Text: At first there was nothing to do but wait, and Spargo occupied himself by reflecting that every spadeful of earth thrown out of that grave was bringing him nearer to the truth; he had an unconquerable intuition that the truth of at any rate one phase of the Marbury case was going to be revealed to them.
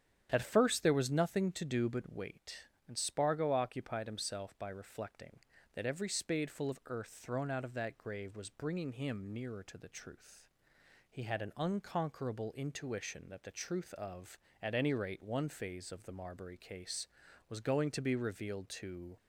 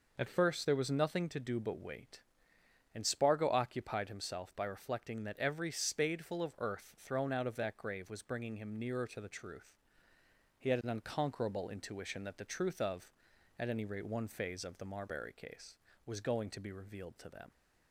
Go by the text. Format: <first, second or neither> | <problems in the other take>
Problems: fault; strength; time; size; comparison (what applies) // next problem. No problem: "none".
second | starts louder than the rest; strong; until 1.3 s; 8.5 dB // stops before "them"; at 19.1 s